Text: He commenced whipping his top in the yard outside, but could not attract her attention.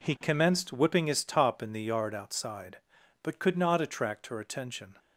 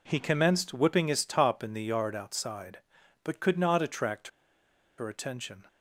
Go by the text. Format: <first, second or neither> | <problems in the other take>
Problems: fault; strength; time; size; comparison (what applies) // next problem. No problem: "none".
first | pauses between "attract" and "her"; noticeable; at 4.2 s; 0.69 s long